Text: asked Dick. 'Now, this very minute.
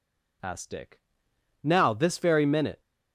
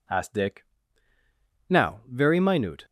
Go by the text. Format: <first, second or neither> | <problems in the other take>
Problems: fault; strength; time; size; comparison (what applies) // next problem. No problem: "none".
first | skips "this"; at 2.0 s